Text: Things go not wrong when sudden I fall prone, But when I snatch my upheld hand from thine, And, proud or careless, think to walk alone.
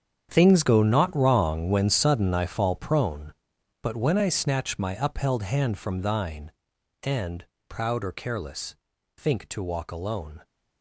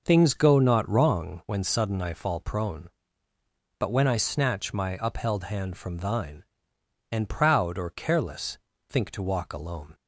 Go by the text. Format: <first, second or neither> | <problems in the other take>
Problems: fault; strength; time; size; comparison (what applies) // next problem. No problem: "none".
second | gets quieter; strong; throughout; 14 dB